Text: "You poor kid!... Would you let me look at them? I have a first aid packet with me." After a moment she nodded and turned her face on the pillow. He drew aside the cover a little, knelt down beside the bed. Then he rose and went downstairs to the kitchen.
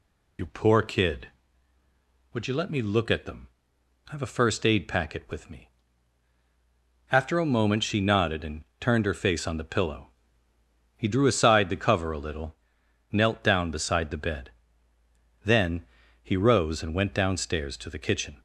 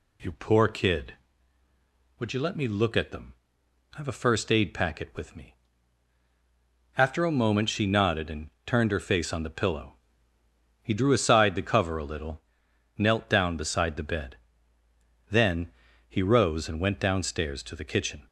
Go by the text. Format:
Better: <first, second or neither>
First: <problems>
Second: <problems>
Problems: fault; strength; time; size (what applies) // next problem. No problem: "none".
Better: second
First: loses the start of "You"; at 0.3 s; 50 ms // pauses between "and" and "turned"; slight; at 8.6 s; 0.16 s long // pauses between "Then" and "he"; slight; at 15.8 s; 0.36 s long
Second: pauses between "and" and "turned"; slight; at 8.5 s; 0.16 s long // pauses between "Then" and "he"; slight; at 15.7 s; 0.36 s long